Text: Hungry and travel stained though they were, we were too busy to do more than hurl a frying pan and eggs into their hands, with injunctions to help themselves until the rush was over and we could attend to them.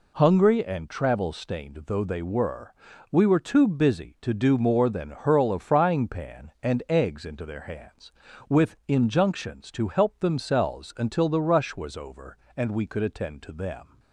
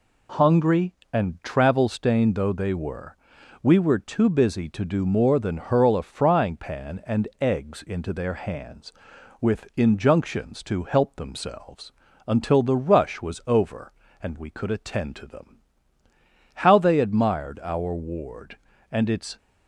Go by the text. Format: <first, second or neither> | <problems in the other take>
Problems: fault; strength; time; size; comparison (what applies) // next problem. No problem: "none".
first | pauses between "themselves" and "until"; at 11.9 s; 0.38 s long // goes on to say "How they admired our ward and its"; strong; from 16.5 s on; 2.8 s long